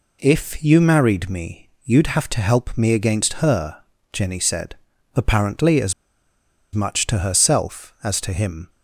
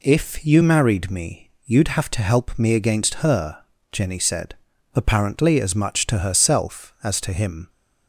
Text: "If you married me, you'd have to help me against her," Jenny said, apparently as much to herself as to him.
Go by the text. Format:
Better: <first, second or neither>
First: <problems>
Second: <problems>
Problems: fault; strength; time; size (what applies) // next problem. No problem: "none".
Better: second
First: pauses between "as" and "much"; noticeable; at 5.9 s; 0.81 s long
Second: none